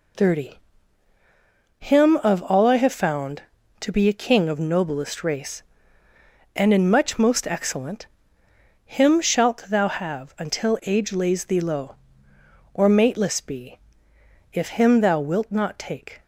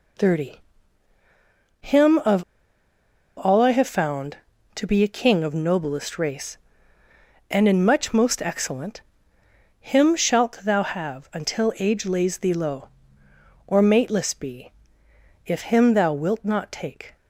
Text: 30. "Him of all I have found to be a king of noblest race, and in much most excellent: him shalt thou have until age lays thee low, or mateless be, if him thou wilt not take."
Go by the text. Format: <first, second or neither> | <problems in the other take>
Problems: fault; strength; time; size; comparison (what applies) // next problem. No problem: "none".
first | pauses between "of" and "all"; noticeable; at 2.4 s; 0.95 s long